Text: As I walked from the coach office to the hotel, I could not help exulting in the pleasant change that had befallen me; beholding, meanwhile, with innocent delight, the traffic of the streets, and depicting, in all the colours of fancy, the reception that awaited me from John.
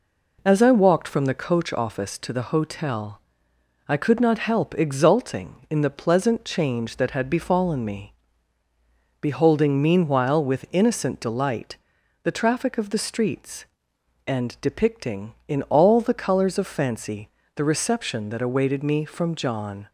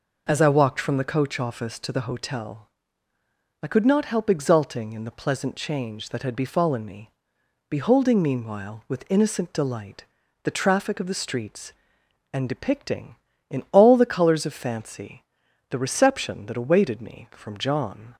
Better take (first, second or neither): neither